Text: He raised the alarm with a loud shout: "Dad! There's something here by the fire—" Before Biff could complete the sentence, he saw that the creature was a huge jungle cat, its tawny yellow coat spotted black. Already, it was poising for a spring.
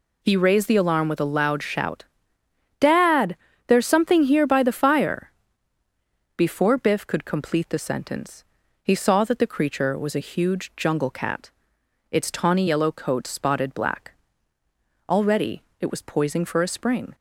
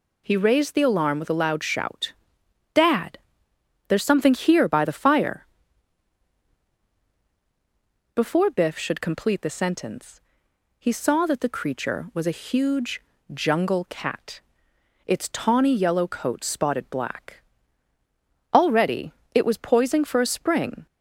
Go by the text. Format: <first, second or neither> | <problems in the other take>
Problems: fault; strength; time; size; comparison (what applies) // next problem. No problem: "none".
first | says "should" for "could"; at 8.7 s // pauses between "huge" and "jungle"; slight; at 13.0 s; 0.32 s long